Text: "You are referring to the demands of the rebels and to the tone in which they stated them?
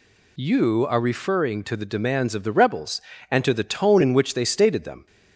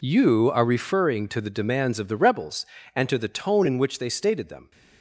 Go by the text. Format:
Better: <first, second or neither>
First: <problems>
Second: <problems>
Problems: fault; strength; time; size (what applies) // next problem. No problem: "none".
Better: first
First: none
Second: gets quieter; strong; throughout; 13 dB